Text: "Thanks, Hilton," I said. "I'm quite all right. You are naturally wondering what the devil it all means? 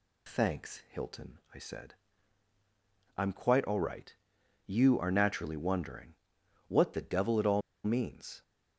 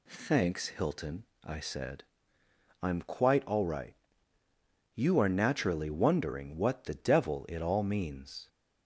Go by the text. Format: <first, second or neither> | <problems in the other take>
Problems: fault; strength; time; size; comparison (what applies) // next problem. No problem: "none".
second | pauses between "wondering" and "what"; noticeable; at 6.1 s; 0.52 s long // pauses between "all" and "means"; slight; at 7.6 s; 0.23 s long